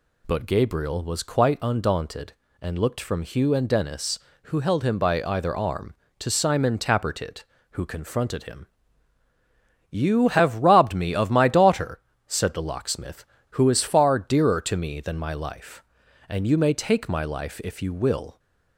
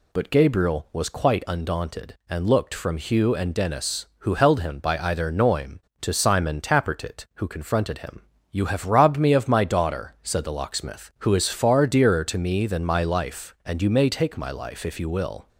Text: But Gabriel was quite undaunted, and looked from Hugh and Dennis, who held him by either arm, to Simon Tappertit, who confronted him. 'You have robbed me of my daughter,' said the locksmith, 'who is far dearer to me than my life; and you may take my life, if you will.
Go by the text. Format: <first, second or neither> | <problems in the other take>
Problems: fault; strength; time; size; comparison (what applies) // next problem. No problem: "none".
first | says "noim" for "arm"; at 5.3 s